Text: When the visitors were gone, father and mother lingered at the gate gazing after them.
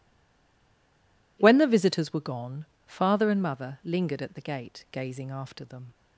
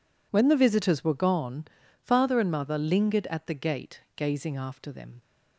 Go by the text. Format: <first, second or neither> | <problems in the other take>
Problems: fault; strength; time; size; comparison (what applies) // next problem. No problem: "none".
second | stays silent before the first word; noticeable; until 1.3 s; 1.3 s long